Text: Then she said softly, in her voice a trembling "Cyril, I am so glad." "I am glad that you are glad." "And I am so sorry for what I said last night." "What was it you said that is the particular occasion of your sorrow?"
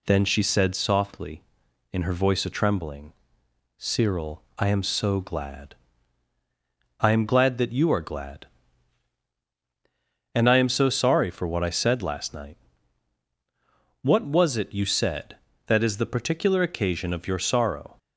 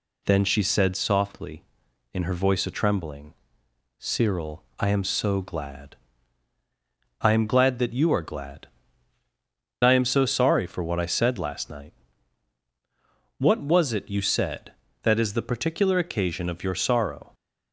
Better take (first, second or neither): first